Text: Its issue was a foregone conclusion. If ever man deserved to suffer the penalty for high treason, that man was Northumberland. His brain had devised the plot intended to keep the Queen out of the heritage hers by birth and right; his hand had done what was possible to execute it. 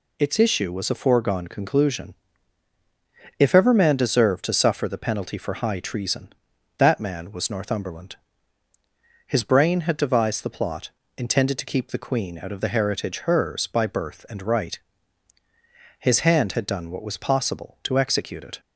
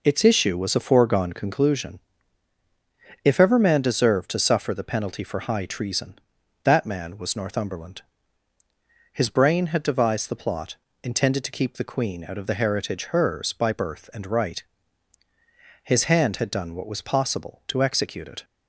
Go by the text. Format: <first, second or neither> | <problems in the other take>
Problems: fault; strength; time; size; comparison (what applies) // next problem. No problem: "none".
first | starts louder than the rest; noticeable; until 1.6 s; 4.5 dB // pauses between "plot" and "intended"; slight; at 10.7 s; 0.28 s long; slight in the first